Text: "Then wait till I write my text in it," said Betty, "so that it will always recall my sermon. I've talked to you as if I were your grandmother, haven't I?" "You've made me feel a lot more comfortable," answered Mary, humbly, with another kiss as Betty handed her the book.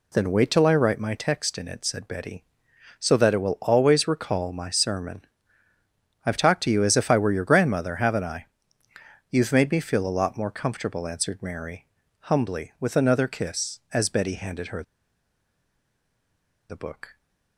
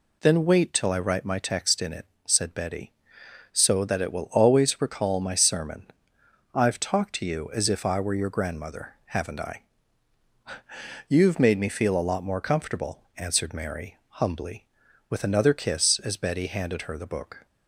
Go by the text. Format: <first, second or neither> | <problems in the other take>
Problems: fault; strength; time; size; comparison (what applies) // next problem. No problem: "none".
second | pauses between "her" and "the"; strong; at 14.8 s; 1.8 s long